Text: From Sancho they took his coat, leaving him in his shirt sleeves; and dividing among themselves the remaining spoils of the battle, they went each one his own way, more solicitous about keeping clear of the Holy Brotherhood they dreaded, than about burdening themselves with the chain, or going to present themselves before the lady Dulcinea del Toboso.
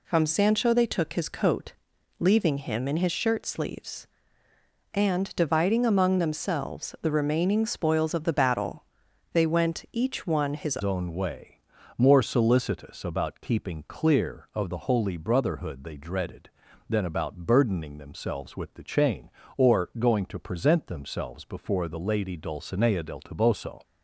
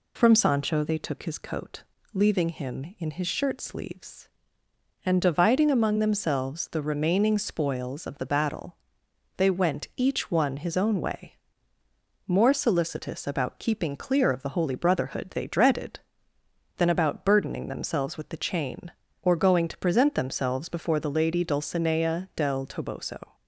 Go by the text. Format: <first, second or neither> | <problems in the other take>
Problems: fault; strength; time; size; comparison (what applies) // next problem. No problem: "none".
second | changes voice at "own"; from 10.8 s on; 13.0 s long